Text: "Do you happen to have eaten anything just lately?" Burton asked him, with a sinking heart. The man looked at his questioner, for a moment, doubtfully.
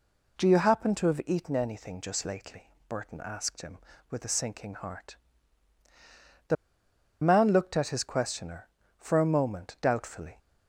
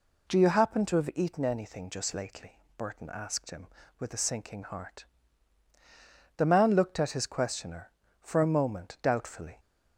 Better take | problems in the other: second | pauses between "The" and "man"; noticeable; at 6.5 s; 0.68 s long

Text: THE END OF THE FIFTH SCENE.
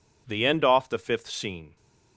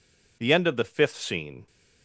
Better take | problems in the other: second | says "Off" for "OF"; at 0.6 s

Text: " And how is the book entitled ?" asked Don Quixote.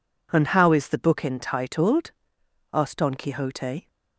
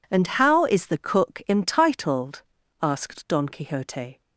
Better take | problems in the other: first | says "cook" for "book"; at 0.9 s

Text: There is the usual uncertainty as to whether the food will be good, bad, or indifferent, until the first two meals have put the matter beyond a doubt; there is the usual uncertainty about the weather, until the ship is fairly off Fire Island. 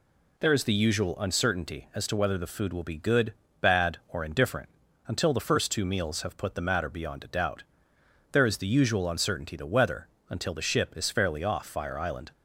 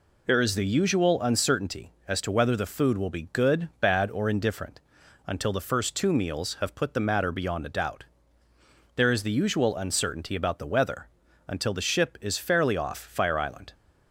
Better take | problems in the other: second | skips "about"; at 9.5 s

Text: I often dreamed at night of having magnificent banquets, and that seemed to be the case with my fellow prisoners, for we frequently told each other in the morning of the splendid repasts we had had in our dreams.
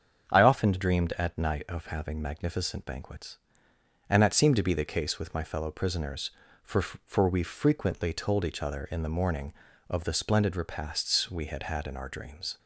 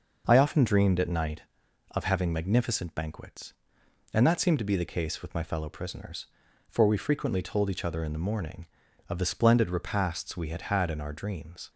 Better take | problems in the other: second | starts louder than the rest; strong; until 1.3 s; 7.5 dB // says "for" twice; at 6.8 s

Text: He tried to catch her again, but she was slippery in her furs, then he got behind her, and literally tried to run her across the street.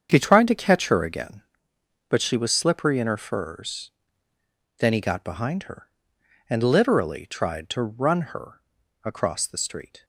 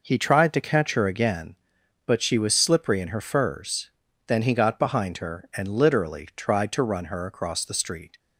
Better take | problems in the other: second | gets quieter; strong; throughout; 11 dB // pauses between "her" and "across"; at 8.6 s; 0.44 s long

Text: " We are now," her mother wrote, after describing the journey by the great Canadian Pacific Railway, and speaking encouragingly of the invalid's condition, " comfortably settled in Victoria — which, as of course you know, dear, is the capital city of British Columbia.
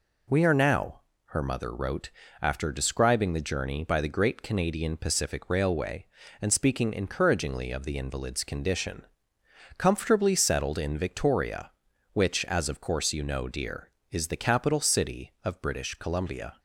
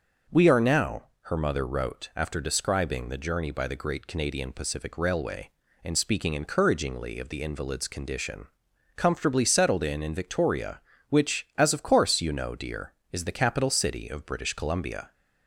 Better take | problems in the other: first | says "in" twice; at 10.0 s

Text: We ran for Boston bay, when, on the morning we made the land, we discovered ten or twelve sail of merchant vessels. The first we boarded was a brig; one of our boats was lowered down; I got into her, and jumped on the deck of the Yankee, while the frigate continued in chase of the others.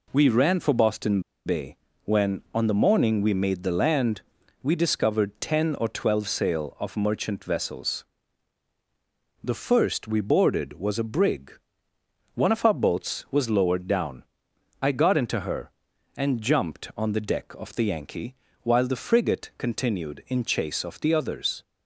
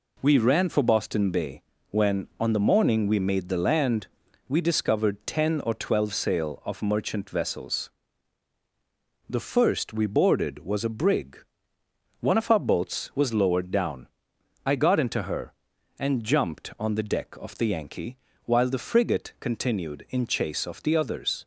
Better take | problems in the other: second | pauses between "Boston" and "bay"; slight; at 1.2 s; 0.25 s long

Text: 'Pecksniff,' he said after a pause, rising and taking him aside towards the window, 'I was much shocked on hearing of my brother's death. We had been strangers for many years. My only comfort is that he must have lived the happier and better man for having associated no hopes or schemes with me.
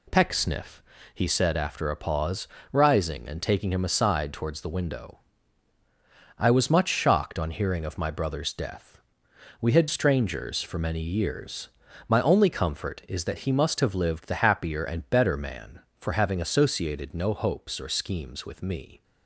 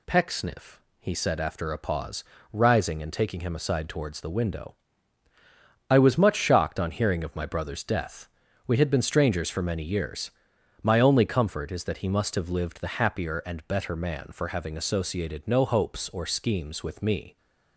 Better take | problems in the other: second | skips "been"; at 9.8 s

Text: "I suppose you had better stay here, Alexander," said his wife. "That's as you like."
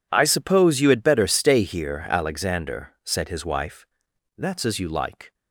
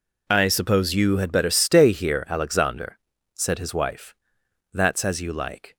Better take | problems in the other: neither | none

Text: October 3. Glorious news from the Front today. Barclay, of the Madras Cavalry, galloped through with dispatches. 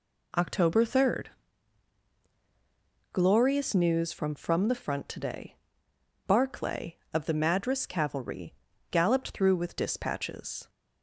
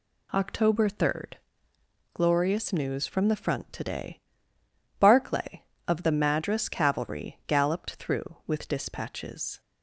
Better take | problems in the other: second | says "from" twice; at 4.3 s

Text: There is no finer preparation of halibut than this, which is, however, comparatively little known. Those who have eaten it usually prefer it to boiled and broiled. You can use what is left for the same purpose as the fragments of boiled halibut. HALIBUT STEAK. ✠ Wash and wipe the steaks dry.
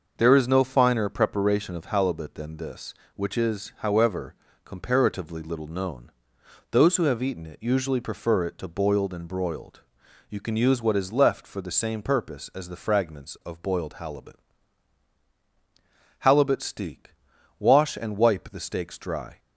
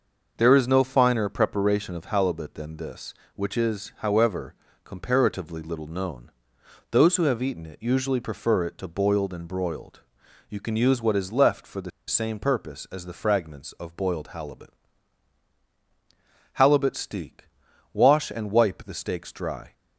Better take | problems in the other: first | starts louder than the rest; noticeable; until 1.3 s; 6 dB; noticeable in the first // pauses between "the" and "same"; slight; at 11.9 s; 0.18 s long

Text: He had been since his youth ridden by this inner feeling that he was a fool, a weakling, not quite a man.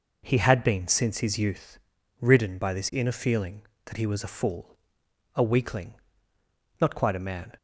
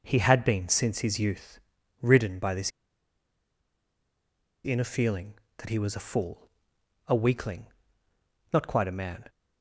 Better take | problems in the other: first | pauses between "youth" and "ridden"; at 1.5 s; 0.40 s long; also in the first // pauses between "this" and "inner"; strong; at 2.7 s; 1.9 s long

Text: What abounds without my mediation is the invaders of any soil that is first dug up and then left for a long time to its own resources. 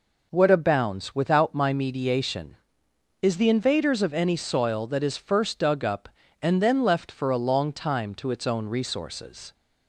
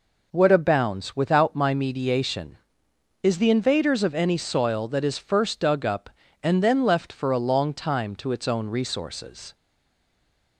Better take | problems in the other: first | stays silent after the last word; from 9.5 s on; 1.0 s long

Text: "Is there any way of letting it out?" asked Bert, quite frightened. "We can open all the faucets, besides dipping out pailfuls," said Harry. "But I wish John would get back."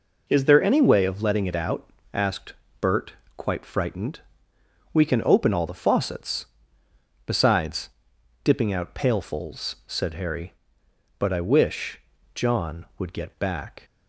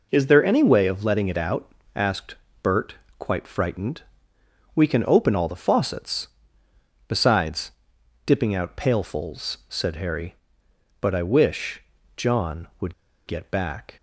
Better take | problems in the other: first | pauses between "asked" and "Bert"; slight; at 2.3 s; 0.28 s long; slight in the first // pauses between "besides" and "dipping"; noticeable; at 7.7 s; 0.54 s long; noticeable in the first // pauses between "wish" and "John"; slight; at 11.8 s; 0.32 s long; slight in the first // pauses between "would" and "get"; slight; at 12.9 s; 0.33 s long

